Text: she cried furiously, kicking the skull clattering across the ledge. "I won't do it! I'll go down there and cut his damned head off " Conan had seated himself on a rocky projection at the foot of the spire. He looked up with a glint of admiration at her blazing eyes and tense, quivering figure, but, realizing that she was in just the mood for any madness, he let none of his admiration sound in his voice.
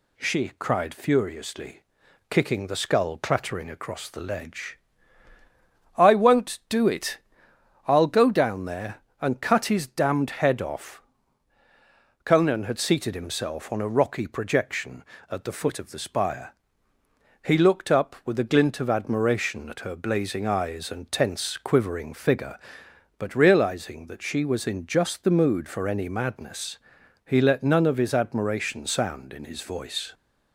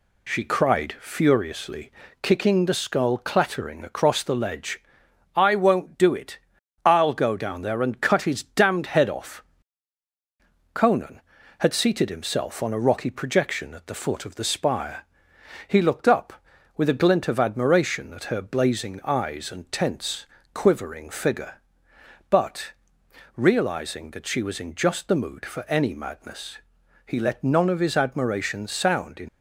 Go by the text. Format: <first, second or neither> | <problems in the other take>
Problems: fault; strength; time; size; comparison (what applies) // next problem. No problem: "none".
first | stops before "his voice"; at 29.2 s